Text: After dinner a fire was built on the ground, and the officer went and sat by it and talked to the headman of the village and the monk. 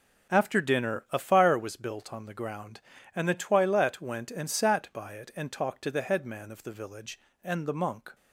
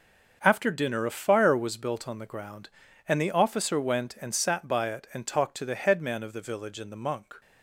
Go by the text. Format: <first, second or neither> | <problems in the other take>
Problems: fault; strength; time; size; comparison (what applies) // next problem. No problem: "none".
second | starts louder than the rest; until 1.3 s; 6.5 dB; also in the second // says "toilette" for "officer"; at 3.3 s